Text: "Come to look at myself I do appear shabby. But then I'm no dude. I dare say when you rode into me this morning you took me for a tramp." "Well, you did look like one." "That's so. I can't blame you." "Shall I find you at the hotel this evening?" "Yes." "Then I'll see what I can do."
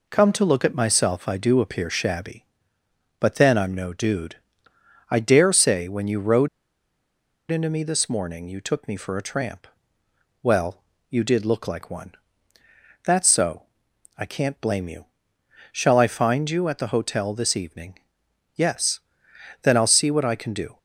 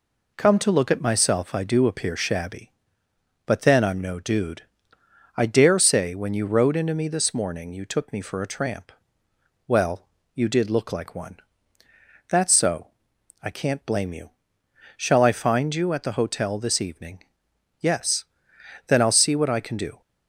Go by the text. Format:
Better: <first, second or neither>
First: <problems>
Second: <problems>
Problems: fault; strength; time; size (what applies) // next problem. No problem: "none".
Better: second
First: pauses between "rode" and "into"; at 6.4 s; 1.0 s long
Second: none